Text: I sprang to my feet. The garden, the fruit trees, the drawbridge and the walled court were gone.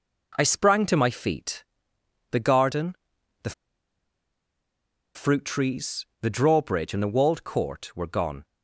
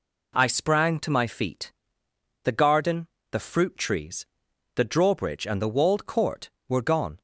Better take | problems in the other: second | pauses between "the" and "fruit"; strong; at 3.5 s; 1.6 s long

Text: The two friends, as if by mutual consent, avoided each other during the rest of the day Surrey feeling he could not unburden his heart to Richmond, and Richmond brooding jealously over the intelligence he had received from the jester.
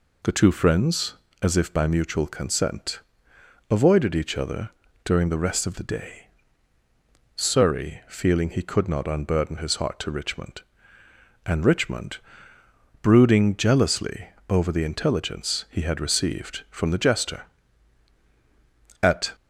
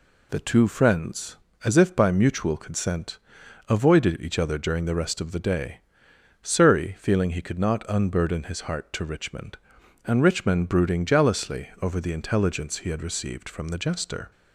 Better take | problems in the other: second | pauses between "other" and "during"; slight; at 4.6 s; 0.34 s long // pauses between "day" and "Surrey"; at 6.2 s; 1.0 s long; noticeable in the second // pauses between "Richmond" and "brooding"; noticeable; at 12.1 s; 0.82 s long // pauses between "jealously" and "over"; slight; at 14.2 s; 0.20 s long // goes on to say "At"; slight; from 19.0 s on; 0.30 s long

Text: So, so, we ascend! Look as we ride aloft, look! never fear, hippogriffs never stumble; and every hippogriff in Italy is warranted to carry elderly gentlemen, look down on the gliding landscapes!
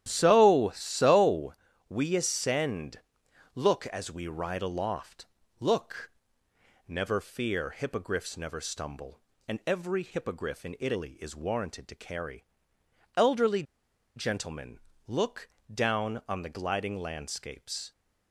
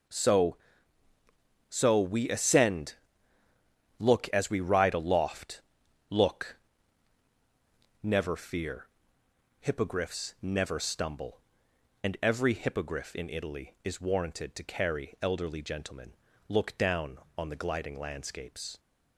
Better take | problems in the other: second | starts louder than the rest; strong; until 1.0 s; 11 dB // pauses between "carry" and "elderly"; noticeable; at 12.4 s; 0.72 s long // pauses between "elderly" and "gentlemen"; noticeable; at 13.6 s; 0.52 s long // pauses between "look" and "down"; slight; at 15.4 s; 0.24 s long

